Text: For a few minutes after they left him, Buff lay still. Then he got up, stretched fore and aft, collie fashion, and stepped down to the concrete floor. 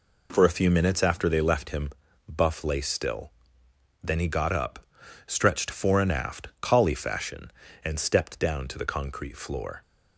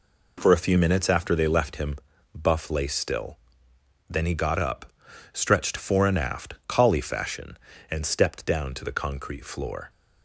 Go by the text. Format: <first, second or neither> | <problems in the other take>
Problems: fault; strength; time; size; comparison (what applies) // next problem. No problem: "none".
neither | none